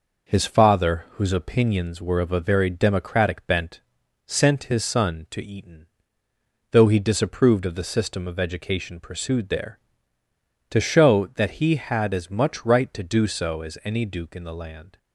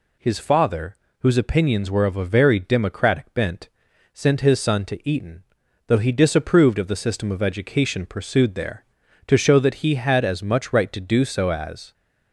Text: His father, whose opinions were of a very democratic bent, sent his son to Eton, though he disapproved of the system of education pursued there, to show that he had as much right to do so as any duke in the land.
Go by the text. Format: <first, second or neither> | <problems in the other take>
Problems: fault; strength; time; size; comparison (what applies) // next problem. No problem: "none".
first | stops before "any duke in the land"; at 11.9 s